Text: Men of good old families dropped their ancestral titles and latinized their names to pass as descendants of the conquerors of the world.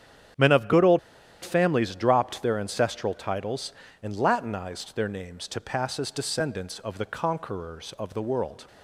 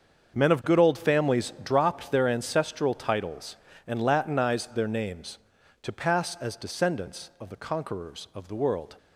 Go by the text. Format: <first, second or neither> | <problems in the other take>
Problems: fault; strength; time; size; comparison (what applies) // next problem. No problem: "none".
second | starts louder than the rest; strong; until 1.8 s; 9 dB; also in the second // pauses between "old" and "families"; at 0.9 s; 0.43 s long